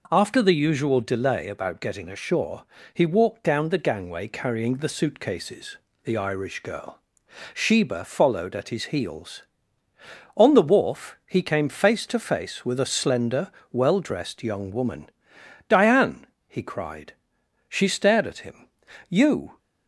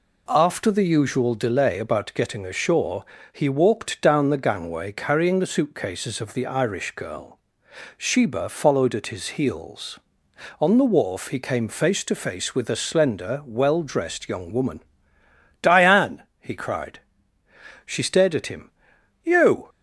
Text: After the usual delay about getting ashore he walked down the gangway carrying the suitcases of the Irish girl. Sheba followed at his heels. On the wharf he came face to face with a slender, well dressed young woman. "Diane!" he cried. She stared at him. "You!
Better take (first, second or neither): second